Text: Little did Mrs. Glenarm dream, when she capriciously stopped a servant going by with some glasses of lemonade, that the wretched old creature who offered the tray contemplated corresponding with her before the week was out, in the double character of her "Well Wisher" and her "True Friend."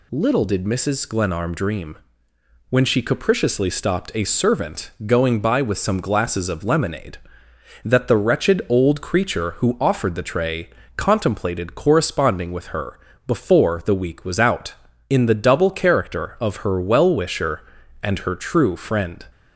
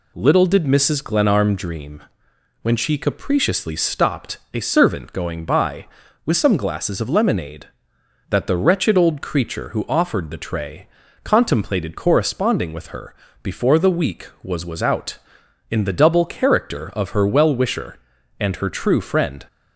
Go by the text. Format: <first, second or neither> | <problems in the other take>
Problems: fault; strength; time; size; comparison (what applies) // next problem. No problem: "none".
first | pauses between "stopped" and "a"; slight; at 4.3 s; 0.16 s long // pauses between "tray" and "contemplated"; at 10.8 s; 0.38 s long; slight in the first // pauses between "her" and "before"; slight; at 13.1 s; 0.28 s long; slight in the first // says "was" twice; at 14.6 s